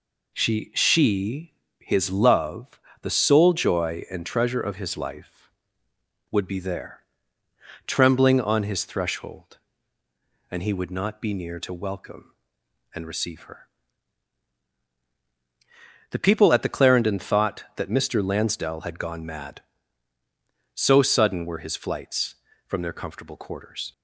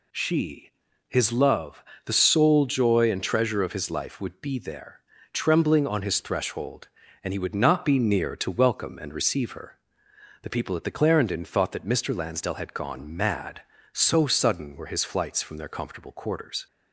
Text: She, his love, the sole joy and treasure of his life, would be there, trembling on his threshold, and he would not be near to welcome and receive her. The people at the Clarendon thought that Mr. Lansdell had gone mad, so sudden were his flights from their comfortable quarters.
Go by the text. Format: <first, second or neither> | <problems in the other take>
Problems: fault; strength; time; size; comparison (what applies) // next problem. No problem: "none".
second | says "She" twice; at 0.7 s